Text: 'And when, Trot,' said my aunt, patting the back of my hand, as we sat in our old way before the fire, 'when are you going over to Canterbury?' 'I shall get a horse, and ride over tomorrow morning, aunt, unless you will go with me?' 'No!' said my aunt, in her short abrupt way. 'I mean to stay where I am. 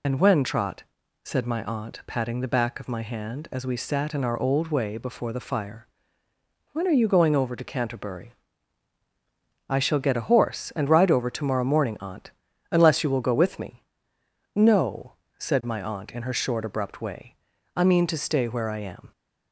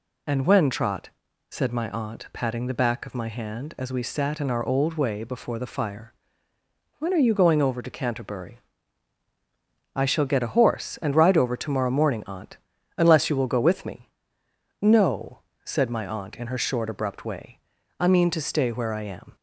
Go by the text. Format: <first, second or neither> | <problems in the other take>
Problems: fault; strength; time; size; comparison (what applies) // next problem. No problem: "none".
second | loses the start of "And"; at 0.0 s; 50 ms